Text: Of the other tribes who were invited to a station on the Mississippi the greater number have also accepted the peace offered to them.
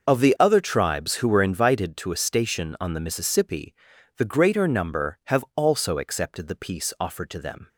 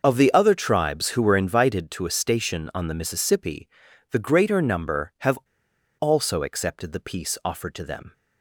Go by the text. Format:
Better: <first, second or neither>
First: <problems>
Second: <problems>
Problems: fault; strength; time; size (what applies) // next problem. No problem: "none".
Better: first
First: pauses between "Mississippi" and "the"; at 3.7 s; 0.44 s long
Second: starts louder than the rest; noticeable; until 1.0 s; 6 dB // pauses between "Mississippi" and "the"; at 3.6 s; 0.44 s long // pauses between "have" and "also"; noticeable; at 5.3 s; 0.64 s long